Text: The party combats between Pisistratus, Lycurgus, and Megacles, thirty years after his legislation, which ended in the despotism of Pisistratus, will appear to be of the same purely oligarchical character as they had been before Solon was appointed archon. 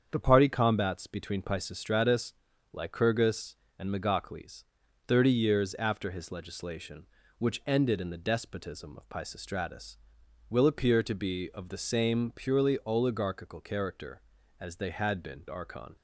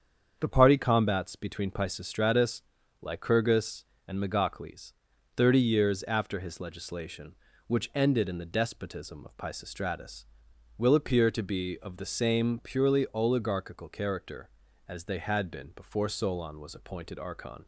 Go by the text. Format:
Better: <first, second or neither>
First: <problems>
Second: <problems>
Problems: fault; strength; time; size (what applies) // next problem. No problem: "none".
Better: second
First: starts louder than the rest; strong; until 1.1 s; 7.5 dB // skips "before Solon was appointed"; at 15.4 s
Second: starts louder than the rest; strong; until 1.4 s; 7.5 dB